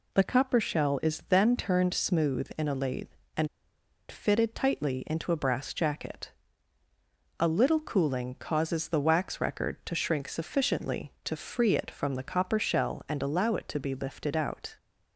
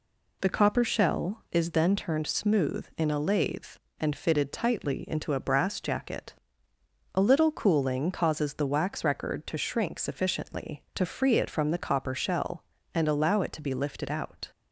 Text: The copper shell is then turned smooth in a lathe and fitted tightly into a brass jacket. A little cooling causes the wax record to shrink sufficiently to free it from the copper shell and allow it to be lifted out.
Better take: second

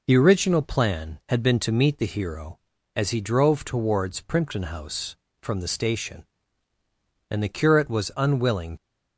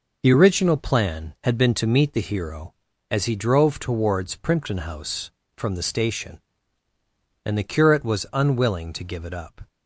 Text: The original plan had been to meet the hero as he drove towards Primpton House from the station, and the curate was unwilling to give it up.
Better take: second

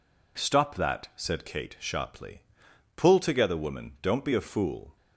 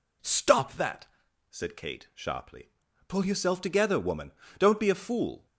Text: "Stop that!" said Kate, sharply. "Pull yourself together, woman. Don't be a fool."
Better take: second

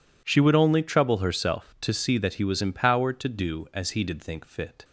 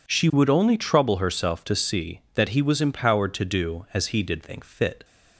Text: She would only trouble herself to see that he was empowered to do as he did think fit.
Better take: neither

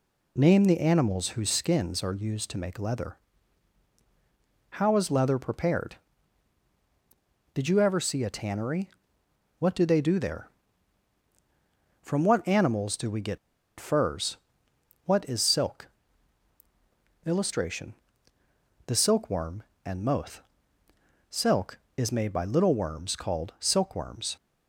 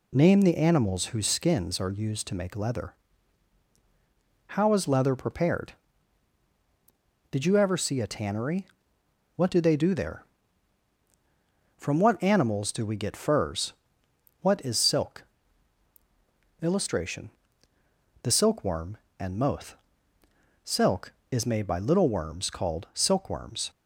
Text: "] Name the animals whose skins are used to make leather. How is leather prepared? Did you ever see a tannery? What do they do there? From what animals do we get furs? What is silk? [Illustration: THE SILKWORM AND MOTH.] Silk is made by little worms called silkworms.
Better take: second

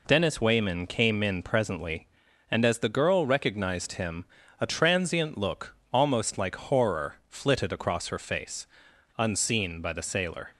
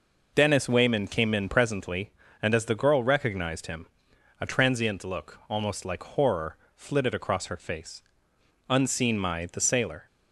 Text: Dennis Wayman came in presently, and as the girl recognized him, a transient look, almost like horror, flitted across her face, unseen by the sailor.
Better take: first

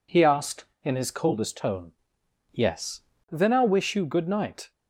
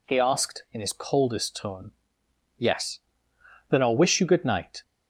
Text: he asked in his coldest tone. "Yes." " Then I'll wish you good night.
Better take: neither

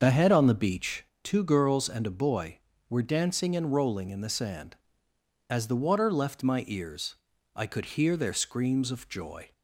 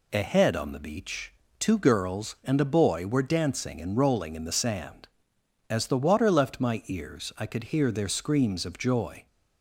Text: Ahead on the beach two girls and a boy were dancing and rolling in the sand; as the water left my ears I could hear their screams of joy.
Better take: second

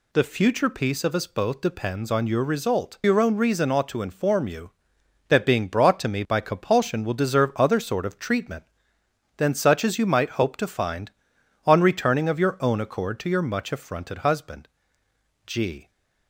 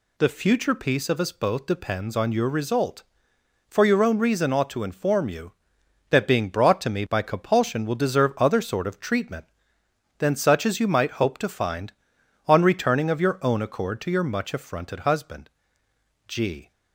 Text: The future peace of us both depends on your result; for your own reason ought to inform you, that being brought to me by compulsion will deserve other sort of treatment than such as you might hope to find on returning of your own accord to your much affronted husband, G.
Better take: second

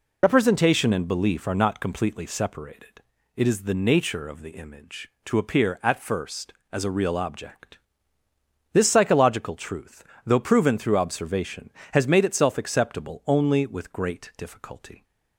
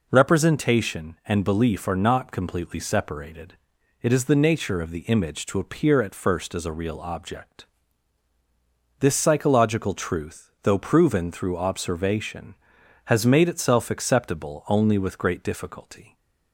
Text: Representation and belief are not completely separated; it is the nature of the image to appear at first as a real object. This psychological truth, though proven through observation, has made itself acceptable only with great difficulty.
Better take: second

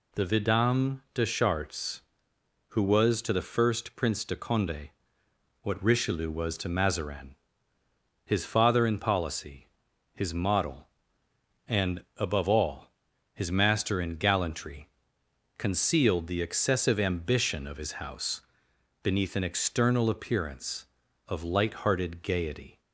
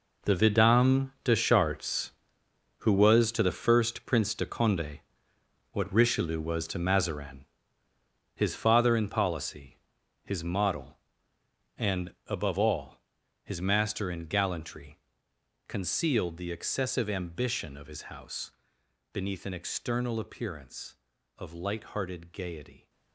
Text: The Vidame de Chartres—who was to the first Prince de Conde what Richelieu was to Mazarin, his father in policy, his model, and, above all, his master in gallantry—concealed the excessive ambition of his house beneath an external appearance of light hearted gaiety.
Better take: first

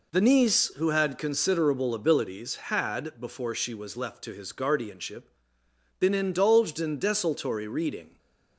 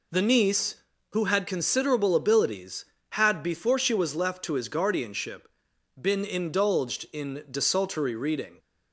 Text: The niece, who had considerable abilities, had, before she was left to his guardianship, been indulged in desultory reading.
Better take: neither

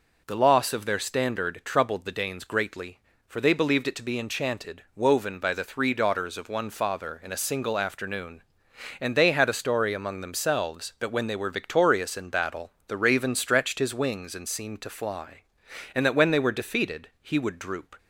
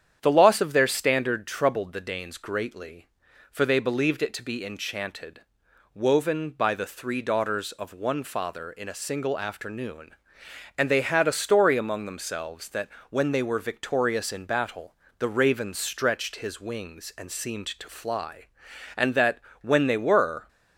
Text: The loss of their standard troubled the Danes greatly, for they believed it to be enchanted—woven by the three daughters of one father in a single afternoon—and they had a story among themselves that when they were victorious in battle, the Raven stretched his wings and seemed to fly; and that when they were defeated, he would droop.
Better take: first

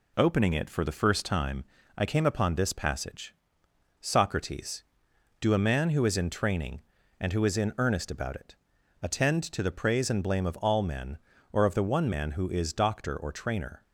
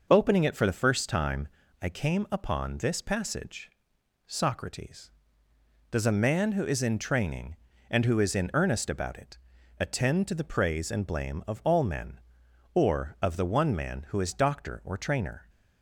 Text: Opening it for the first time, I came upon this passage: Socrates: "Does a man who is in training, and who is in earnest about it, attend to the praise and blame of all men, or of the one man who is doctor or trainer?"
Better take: second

